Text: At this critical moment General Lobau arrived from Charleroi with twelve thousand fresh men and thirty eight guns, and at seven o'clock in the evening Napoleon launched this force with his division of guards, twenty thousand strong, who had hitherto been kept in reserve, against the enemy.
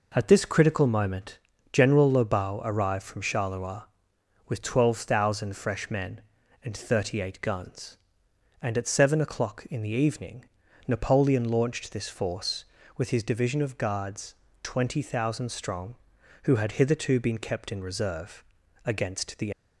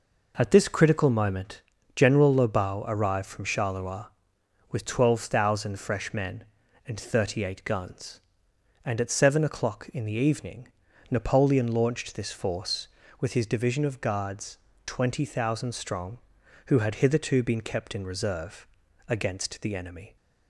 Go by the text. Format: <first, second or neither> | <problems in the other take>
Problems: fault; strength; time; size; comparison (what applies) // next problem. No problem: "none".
second | pauses between "moment" and "General"; slight; at 1.3 s; 0.34 s long; slight in the second // pauses between "evening" and "Napoleon"; at 10.4 s; 0.42 s long; also in the second // stops before "enemy"; at 19.5 s